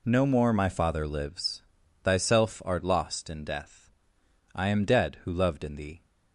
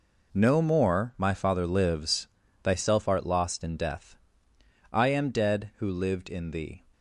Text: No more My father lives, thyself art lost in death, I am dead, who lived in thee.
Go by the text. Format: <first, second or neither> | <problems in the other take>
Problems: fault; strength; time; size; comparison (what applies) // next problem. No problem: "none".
second | says "loved" for "lived"; at 5.3 s